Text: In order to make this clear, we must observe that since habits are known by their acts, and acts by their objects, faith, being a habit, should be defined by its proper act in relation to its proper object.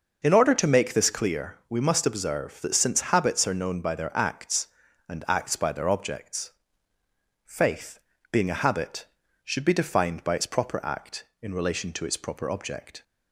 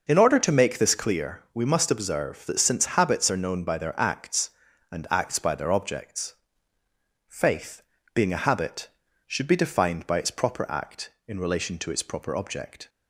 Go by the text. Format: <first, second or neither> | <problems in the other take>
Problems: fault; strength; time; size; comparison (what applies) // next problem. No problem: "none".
neither | none